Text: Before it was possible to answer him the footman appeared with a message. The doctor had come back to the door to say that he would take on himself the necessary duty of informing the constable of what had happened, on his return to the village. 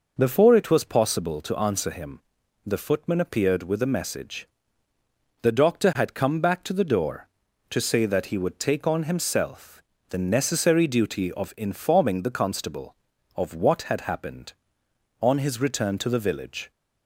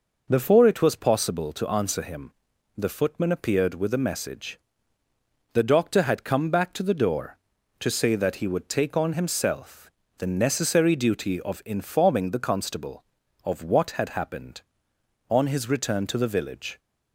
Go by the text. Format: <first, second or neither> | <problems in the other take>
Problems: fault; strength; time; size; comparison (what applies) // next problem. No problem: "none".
neither | pauses between "him" and "the"; noticeable; the same in both // pauses between "himself" and "the"; slight; the same in both